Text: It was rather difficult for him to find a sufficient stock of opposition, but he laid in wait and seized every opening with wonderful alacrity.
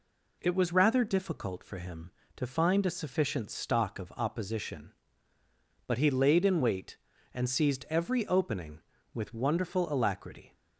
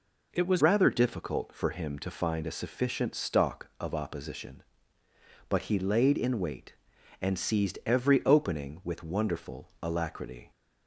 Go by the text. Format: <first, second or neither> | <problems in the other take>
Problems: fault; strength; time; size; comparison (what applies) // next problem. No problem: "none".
first | changes voice at "rather"; from 0.6 s on; 9.9 s long